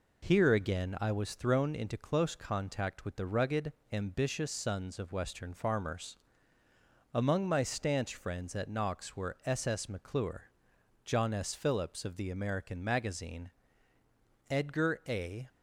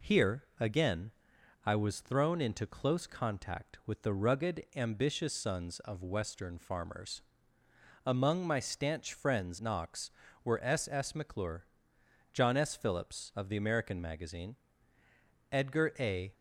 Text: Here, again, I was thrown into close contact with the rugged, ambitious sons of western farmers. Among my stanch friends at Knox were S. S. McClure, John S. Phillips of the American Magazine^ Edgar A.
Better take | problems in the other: first | skips "at"; at 9.5 s // pauses between "Magazine" and "Edgar"; noticeable; at 14.5 s; 0.96 s long; noticeable in the first

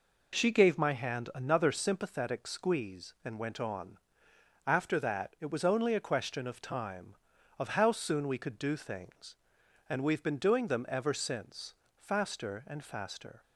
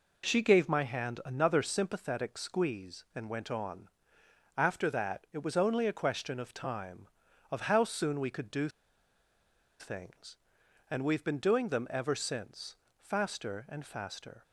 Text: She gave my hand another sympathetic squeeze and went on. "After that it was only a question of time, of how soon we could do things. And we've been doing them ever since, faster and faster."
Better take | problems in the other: first | pauses between "do" and "things"; at 8.6 s; 1.1 s long

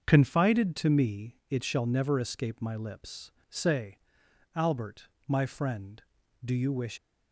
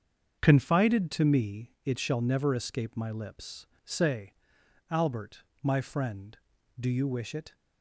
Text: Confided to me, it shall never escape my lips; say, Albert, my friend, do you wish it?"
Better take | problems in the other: second | starts louder than the rest; until 1.0 s; 6.5 dB; also in the second // stops before "it"; at 6.9 s

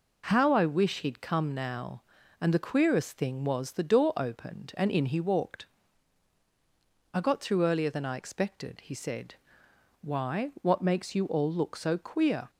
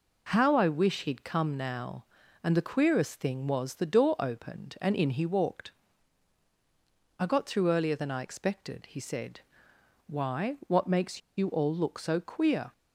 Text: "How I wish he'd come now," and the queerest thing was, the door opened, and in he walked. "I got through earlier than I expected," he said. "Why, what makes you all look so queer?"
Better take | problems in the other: first | pauses between "makes" and "you"; slight; at 11.2 s; 0.18 s long

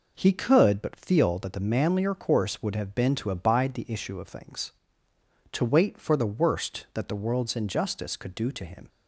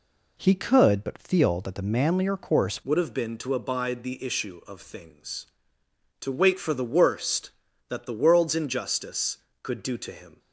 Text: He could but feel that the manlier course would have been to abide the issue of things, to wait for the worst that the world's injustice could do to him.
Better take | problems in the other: first | changes voice at "would"; from 2.8 s on; 7.5 s long

